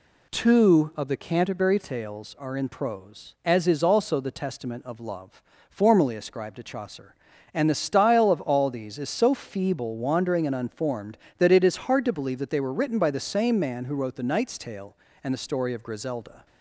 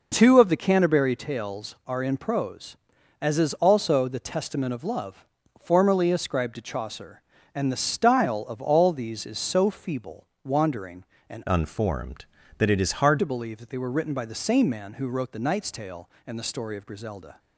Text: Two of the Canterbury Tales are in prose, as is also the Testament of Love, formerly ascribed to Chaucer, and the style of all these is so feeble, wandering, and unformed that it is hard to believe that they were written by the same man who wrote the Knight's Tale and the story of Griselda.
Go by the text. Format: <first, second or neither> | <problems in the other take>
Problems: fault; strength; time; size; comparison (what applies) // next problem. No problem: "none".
first | changes voice from "unformed" to "hard"; from 11.4 to 13.1 s; 1.7 s long